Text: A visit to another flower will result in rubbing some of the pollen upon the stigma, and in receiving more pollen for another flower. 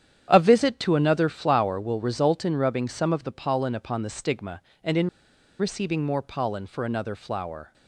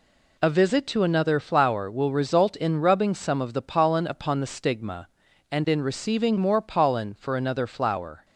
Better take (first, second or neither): second